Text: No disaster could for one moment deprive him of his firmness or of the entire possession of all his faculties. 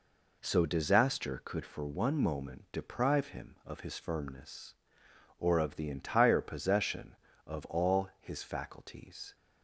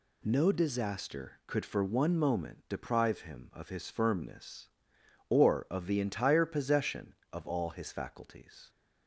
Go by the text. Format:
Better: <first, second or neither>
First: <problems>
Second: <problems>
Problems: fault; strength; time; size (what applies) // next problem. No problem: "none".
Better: second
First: says "So" for "No"; at 0.4 s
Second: none